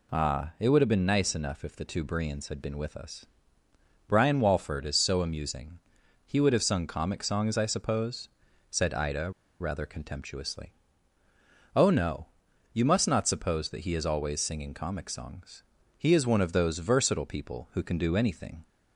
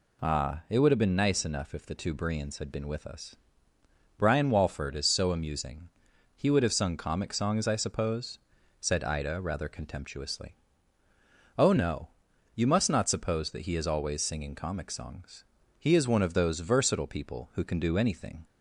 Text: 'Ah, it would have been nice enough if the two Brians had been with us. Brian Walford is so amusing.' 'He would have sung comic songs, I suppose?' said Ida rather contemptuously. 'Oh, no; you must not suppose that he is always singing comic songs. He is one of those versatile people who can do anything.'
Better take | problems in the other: second | pauses between "Ida" and "rather"; slight; at 9.3 s; 0.28 s long

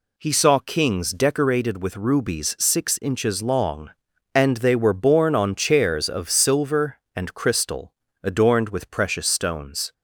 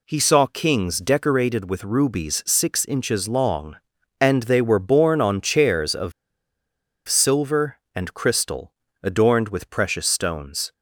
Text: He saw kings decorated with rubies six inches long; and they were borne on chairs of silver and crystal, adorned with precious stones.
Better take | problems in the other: first | pauses between "of" and "silver"; noticeable; at 6.1 s; 0.95 s long

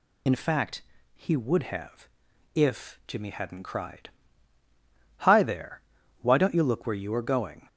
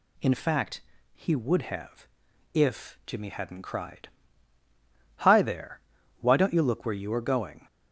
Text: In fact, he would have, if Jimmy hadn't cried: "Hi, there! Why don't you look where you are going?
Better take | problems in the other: second | loses the start of "In"; at 0.2 s; 75 ms

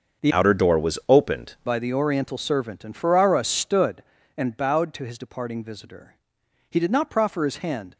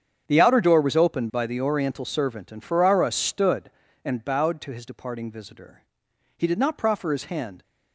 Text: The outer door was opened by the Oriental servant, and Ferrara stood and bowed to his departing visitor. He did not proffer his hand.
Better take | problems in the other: second | starts louder than the rest; until 1.3 s; 6.5 dB; strong in the second // changes voice from "outer" to "opened"; from 0.3 to 1.5 s; 1.2 s long

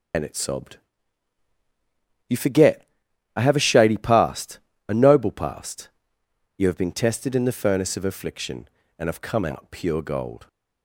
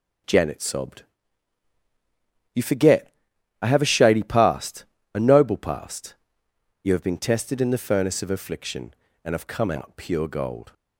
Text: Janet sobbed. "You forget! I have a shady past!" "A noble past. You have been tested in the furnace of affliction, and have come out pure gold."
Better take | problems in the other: second | loses the start of "Janet"; at 0.1 s; 155 ms // starts louder than the rest; until 2.6 s; 6.5 dB

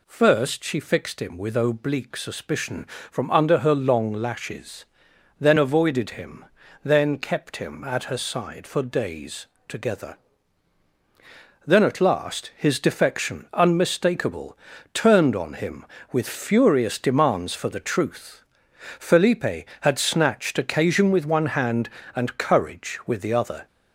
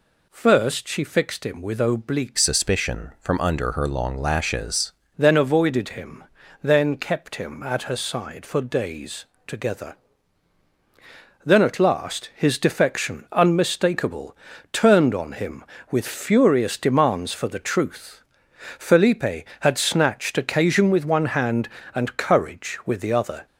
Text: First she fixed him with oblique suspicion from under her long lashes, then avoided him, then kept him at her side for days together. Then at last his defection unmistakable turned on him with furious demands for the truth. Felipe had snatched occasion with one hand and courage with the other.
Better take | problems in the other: first | changes voice from "suspicion" to "lashes"; from 2.3 to 4.9 s; 2.6 s long // pauses between "days" and "together"; slight; at 9.2 s; 0.20 s long; slight in the first // pauses between "unmistakable" and "turned"; slight; at 14.3 s; 0.36 s long; slight in the first

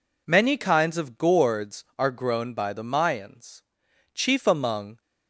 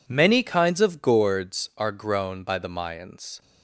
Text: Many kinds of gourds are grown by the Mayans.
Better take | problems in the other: second | goes on to say "Chief among"; noticeable; from 4.1 s on; 0.88 s long

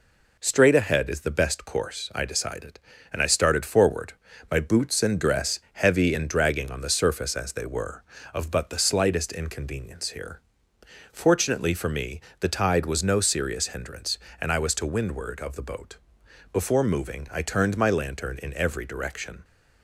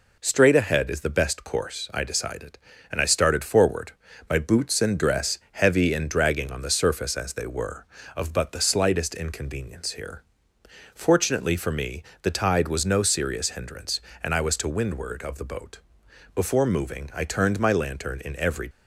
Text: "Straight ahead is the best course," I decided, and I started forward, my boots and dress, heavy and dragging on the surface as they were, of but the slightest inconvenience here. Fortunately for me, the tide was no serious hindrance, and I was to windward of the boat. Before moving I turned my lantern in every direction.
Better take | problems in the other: first | stops before "direction"; at 18.7 s

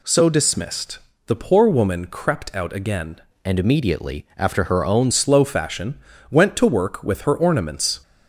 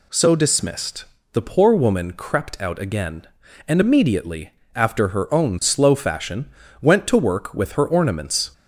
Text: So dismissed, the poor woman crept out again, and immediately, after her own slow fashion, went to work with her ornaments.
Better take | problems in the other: second | changes voice from "and" to "own"; from 3.4 to 5.1 s; 1.7 s long

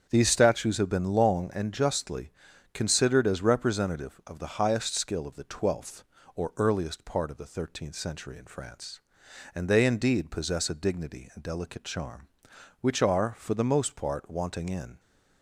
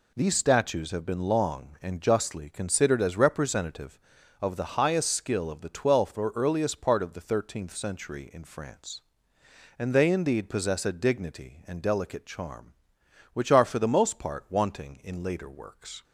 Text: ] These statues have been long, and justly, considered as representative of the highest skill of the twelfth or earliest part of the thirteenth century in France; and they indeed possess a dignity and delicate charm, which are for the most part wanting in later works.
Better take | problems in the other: second | starts louder than the rest; strong; until 1.1 s; 8 dB // stops before "later works"; at 14.9 s

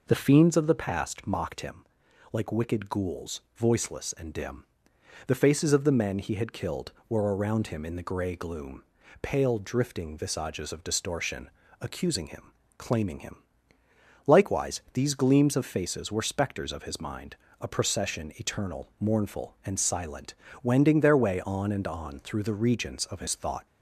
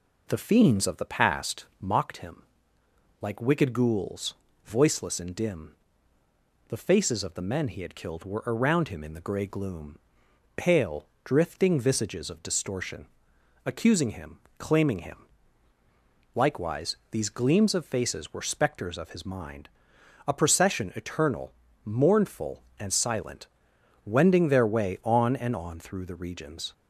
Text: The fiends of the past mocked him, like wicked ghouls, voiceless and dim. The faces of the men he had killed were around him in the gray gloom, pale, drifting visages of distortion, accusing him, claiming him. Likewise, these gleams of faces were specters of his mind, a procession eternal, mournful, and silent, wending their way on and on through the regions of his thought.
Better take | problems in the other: first | stops before "of his thought"; at 26.7 s

